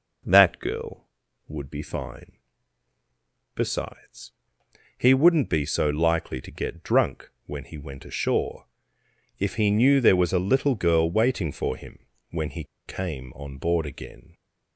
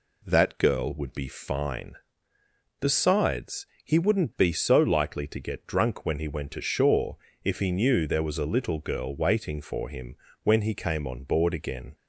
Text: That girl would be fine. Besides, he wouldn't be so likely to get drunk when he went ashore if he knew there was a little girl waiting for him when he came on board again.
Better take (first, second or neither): second